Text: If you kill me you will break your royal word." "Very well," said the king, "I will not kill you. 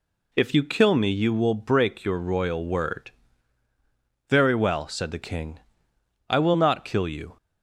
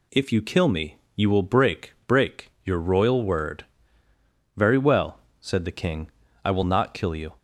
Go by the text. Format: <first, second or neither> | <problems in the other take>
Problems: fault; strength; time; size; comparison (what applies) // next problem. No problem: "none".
first | pauses between "me" and "you"; slight; at 0.9 s; 0.20 s long // says "break" twice; at 2.0 s